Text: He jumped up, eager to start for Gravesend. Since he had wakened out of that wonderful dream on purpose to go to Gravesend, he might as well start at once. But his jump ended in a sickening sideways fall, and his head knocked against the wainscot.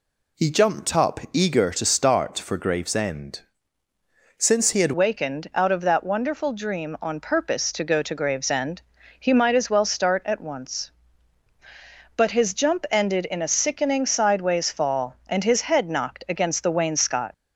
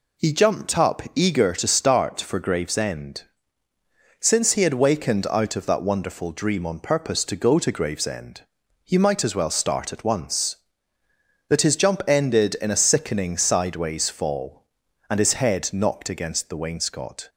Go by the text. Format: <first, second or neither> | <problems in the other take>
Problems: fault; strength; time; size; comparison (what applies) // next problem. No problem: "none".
second | changes voice at "wakened"; from 4.9 s on; 12.4 s long